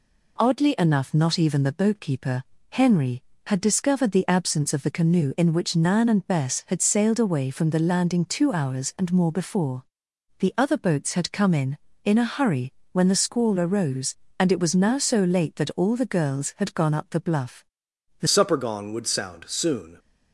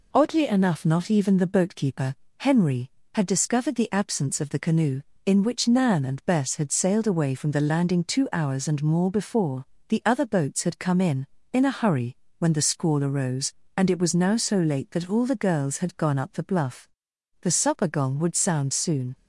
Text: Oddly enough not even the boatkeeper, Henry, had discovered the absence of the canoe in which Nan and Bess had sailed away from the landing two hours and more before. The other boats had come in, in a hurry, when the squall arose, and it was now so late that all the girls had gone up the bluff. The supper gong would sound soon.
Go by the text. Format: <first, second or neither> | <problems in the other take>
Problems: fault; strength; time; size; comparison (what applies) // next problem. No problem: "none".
second | changes voice at "supper"; from 18.2 s on; 1.7 s long